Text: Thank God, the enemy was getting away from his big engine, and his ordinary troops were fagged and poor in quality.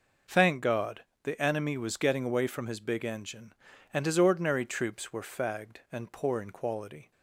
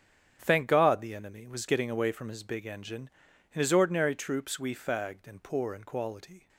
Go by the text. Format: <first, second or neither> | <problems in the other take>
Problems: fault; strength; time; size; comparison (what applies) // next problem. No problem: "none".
first | starts louder than the rest; strong; until 1.4 s; 9 dB // says "we" for "were"; at 4.5 s